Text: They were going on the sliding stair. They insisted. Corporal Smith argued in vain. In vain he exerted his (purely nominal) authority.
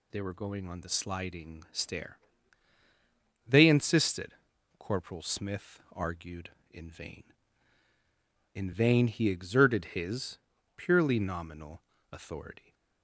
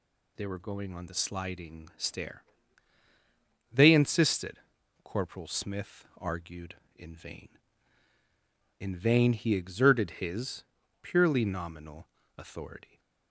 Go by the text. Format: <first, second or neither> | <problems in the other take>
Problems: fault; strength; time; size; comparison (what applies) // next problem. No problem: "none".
neither | none